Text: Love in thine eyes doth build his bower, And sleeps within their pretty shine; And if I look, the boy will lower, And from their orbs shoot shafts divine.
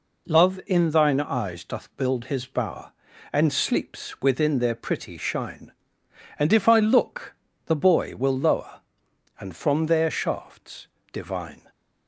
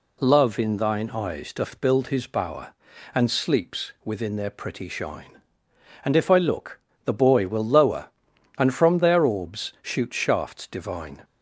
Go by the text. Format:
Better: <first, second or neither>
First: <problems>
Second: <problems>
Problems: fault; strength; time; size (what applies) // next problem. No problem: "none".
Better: second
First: skips "orbs shoot"; at 10.0 s // pauses between "shafts" and "divine"; slight; at 10.8 s; 0.24 s long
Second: none